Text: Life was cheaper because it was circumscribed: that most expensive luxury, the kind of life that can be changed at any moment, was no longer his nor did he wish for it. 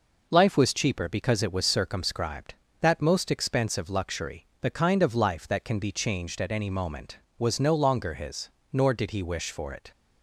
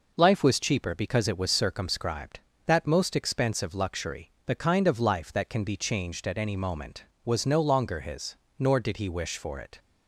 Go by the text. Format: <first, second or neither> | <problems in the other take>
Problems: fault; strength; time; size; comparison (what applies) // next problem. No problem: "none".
neither | pauses between "his" and "nor"; slight; the same in both